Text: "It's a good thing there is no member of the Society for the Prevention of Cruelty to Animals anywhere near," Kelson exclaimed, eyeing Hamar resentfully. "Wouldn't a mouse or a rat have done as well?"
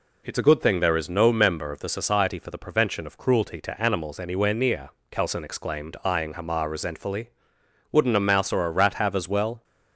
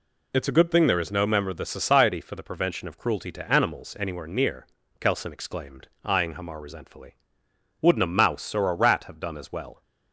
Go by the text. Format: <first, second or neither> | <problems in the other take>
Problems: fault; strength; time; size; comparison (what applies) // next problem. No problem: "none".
second | skips "done"; at 9.1 s